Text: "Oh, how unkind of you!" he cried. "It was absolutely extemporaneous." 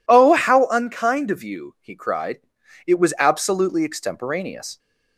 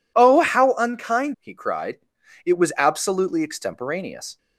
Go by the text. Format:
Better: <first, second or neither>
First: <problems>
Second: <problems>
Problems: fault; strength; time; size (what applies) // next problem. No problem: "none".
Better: first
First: none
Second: skips "of you"; at 1.3 s